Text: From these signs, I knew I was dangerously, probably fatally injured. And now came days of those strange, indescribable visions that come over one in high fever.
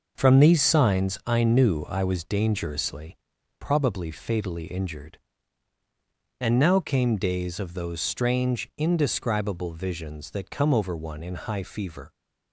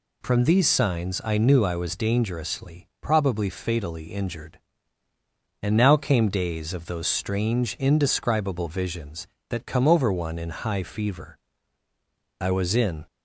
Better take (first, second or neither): first